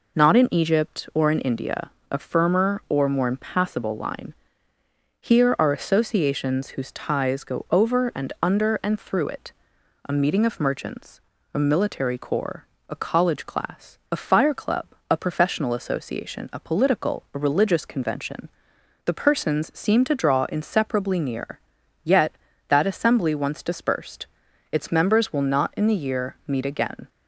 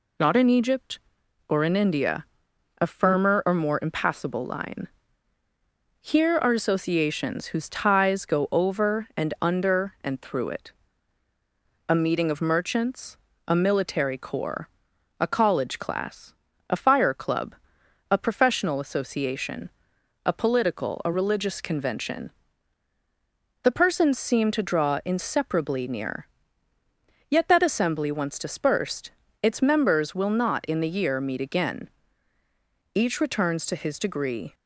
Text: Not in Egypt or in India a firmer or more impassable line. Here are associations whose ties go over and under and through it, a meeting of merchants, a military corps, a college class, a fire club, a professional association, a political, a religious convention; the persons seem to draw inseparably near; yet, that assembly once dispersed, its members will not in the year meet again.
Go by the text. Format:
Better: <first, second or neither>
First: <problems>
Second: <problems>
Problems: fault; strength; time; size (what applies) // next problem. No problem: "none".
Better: first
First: pauses between "India" and "a"; slight; at 1.8 s; 0.22 s long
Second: pauses between "India" and "a"; noticeable; at 2.2 s; 0.56 s long // goes on to say "Each returns to his degree"; from 32.9 s on; 1.5 s long